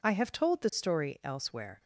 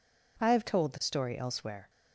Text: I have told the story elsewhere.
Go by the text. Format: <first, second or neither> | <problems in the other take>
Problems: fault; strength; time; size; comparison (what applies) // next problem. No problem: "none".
neither | none